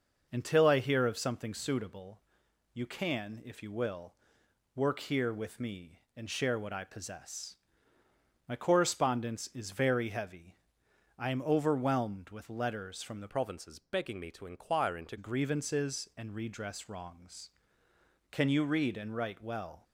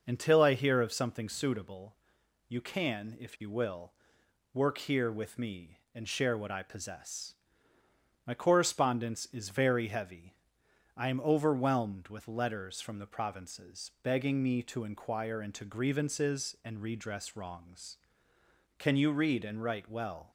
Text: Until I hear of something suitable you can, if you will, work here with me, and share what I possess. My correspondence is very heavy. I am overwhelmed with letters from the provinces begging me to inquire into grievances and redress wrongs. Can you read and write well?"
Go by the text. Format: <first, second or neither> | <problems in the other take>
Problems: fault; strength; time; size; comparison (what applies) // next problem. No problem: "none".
second | pauses between "suitable" and "you"; noticeable; at 2.1 s; 0.54 s long; noticeable in the second // changes voice from "provinces" to "into"; from 13.2 to 15.1 s; 1.9 s long